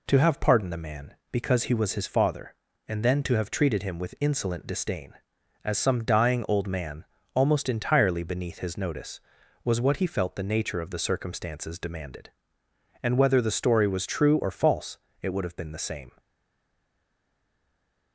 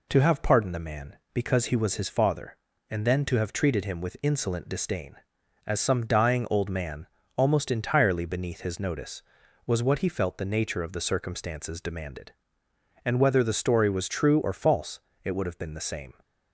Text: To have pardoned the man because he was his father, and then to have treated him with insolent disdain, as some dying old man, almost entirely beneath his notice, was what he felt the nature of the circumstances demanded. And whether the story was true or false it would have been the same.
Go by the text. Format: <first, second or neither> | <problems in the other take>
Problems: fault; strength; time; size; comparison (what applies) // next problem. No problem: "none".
second | pauses between "false" and "it"; slight; at 14.9 s; 0.24 s long; slight in the second // stays silent after the last word; noticeable; from 16.1 s on; 2.0 s long